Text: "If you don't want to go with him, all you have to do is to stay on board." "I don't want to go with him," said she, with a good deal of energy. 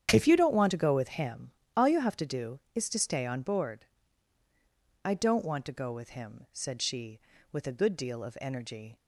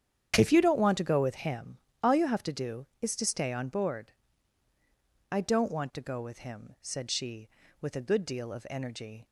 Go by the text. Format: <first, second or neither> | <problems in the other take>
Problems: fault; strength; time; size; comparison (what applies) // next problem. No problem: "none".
neither | starts louder than the rest; strong; the same in both